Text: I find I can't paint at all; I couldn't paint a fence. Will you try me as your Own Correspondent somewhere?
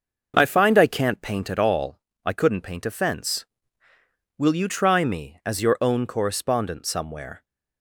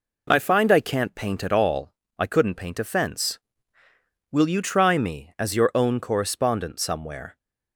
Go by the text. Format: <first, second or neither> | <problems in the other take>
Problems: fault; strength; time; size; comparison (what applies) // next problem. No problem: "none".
second | starts louder than the rest; noticeable; until 1.4 s; 6 dB